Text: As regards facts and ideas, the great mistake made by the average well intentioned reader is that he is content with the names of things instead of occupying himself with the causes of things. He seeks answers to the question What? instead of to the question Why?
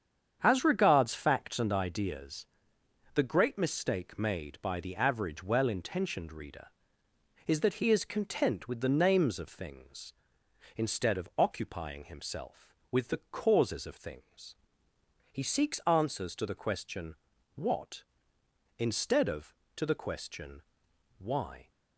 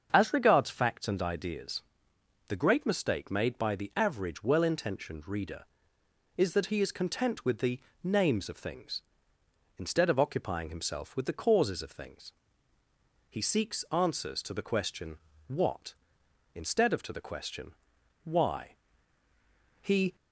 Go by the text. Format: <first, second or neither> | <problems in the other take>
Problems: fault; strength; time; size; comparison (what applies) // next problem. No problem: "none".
first | starts louder than the rest; until 1.1 s; 7 dB; strong in the first // pauses between "the" and "names"; slight; at 7.7 s; 0.24 s long // pauses between "question" and "What"; slight; at 15.1 s; 0.30 s long; also in the first // pauses between "question" and "Why"; noticeable; at 17.7 s; 0.52 s long; noticeable in the first // goes on to say "He"; slight; from 19.8 s on; 0.34 s long